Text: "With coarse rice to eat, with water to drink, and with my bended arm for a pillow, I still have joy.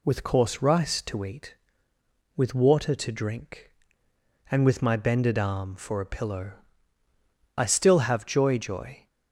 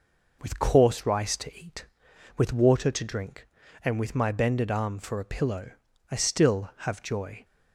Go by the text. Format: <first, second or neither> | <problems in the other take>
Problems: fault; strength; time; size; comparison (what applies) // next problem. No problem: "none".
second | says "joy" twice; at 8.5 s